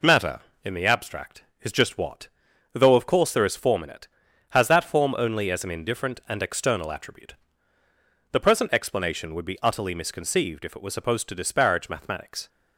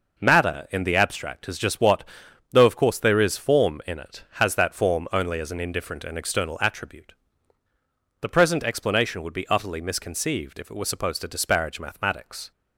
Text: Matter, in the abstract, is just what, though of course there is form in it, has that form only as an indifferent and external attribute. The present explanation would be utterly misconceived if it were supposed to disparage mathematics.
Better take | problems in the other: neither | none

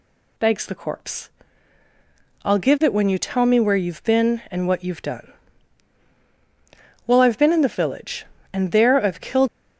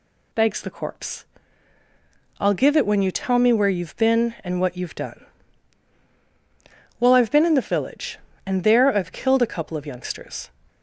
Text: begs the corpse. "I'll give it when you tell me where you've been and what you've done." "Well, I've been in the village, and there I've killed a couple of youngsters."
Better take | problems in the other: second | stops before "a couple of youngsters"; at 9.4 s

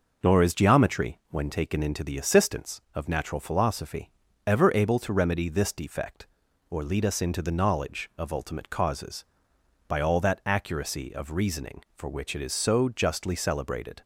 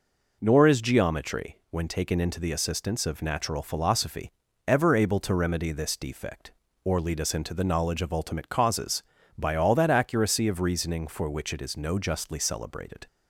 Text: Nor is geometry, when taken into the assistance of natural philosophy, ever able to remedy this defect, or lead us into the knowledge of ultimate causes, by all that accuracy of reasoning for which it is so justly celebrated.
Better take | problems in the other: first | says "no" for "so"; at 11.7 s

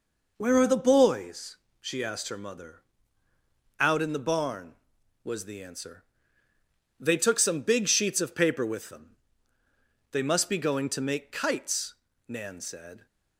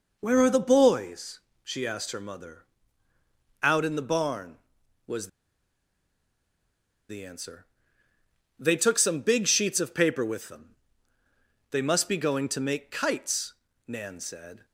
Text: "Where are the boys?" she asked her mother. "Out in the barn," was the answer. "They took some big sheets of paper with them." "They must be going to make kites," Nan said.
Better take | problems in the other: first | pauses between "was" and "the"; strong; at 5.2 s; 1.8 s long

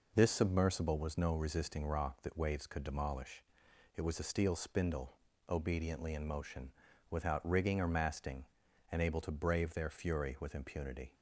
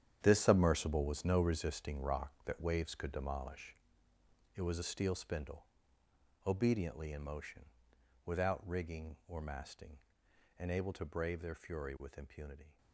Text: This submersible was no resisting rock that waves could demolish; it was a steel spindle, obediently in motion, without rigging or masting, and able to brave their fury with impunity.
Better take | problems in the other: first | gets quieter; strong; throughout; 12.5 dB

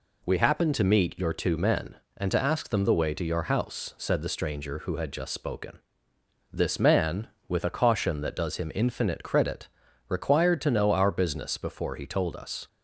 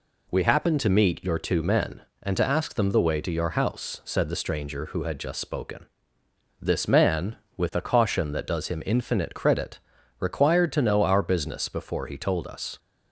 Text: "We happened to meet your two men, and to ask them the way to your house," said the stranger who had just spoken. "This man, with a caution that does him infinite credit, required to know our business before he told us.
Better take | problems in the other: neither | none

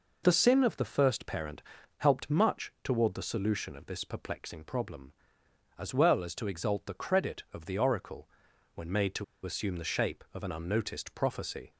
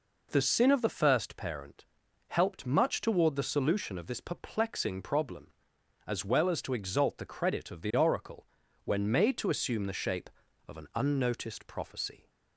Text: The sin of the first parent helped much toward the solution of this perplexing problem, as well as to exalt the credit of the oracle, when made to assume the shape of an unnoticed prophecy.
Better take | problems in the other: second | pauses between "parent" and "helped"; at 1.6 s; 0.38 s long; also in the second // pauses between "to" and "assume"; slight; at 9.2 s; 0.20 s long

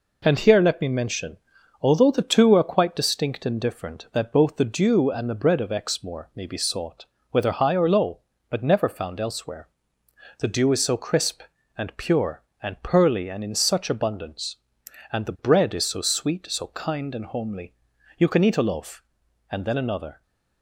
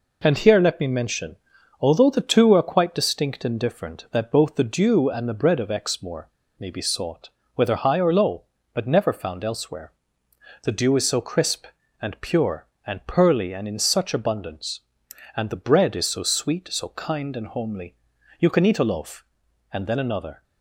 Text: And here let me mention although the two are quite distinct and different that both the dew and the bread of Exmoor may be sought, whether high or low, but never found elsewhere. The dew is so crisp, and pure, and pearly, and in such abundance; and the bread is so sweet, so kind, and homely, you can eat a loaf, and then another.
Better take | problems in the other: first | pauses between "mention" and "although"; at 1.3 s; 0.44 s long; also in the first // pauses between "Exmoor" and "may"; slight; at 6.2 s; 0.29 s long

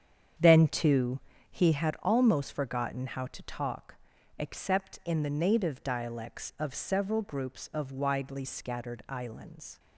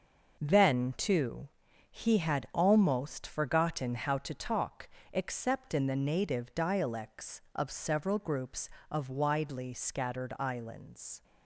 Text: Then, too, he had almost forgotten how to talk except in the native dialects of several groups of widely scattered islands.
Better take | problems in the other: second | starts louder than the rest; strong; until 1.9 s; 8 dB // pauses between "talk" and "except"; at 3.9 s; 0.42 s long; slight in the second

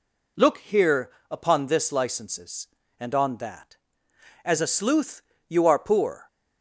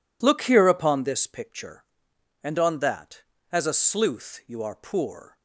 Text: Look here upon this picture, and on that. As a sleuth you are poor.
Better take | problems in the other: second | pauses between "here" and "upon"; slight; at 1.1 s; 0.18 s long // says "licenses" for "picture"; at 1.9 s // pauses between "sleuth" and "you"; slight; at 5.2 s; 0.28 s long

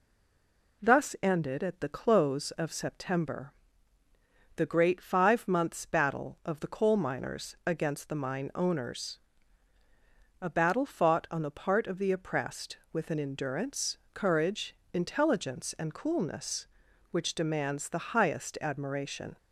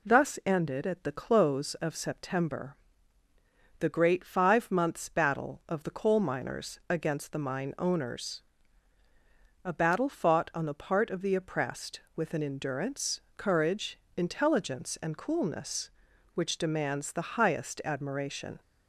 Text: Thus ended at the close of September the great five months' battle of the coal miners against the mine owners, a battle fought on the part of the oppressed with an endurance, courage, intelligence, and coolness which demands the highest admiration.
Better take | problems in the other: second | stays silent before the first word; slight; until 0.8 s; 0.8 s long // pauses between "September" and "the"; at 3.5 s; 1.0 s long; also in the second

